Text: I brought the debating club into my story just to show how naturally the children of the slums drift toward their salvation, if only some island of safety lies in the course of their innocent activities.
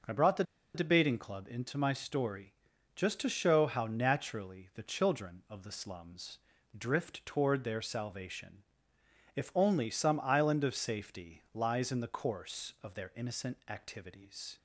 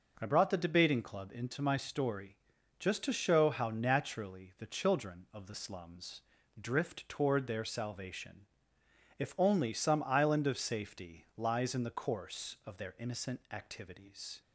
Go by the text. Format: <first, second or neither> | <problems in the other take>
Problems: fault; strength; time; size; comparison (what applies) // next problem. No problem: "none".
second | pauses between "the" and "debating"; slight; at 0.4 s; 0.32 s long // pauses between "story" and "just"; at 2.5 s; 0.42 s long; also in the second // pauses between "slums" and "drift"; at 6.3 s; 0.40 s long; also in the second